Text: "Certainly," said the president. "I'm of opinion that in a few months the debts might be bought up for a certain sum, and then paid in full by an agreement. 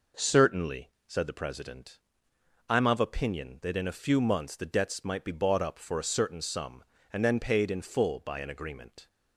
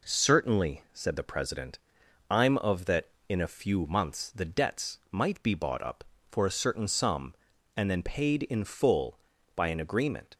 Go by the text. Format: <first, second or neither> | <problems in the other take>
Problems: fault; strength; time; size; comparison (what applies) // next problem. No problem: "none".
first | skips "opinion"; at 2.8 s